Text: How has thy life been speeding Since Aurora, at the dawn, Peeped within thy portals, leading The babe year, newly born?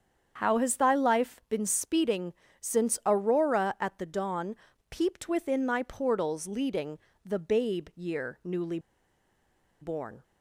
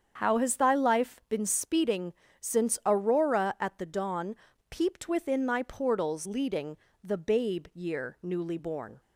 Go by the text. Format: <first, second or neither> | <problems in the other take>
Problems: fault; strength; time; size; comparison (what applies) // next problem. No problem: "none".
second | starts louder than the rest; strong; until 1.3 s; 7.5 dB; strong in the second // pauses between "speeding" and "Since"; slight; at 2.3 s; 0.26 s long; slight in the second // pauses between "leading" and "The"; slight; at 6.9 s; 0.26 s long; slight in the second // pauses between "newly" and "born"; at 8.7 s; 1.0 s long